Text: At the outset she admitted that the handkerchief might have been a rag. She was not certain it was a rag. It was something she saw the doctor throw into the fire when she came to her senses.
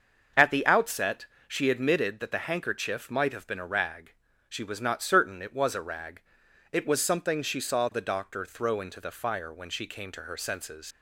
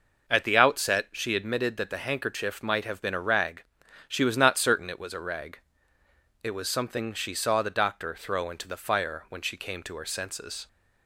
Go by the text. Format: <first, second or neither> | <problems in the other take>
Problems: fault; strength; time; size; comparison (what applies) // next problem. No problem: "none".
second | starts louder than the rest; until 1.5 s; 6.5 dB // pauses between "outset" and "she"; slight; at 1.2 s; 0.20 s long // leaves "senses" unfinished; at 10.9 s; 80 ms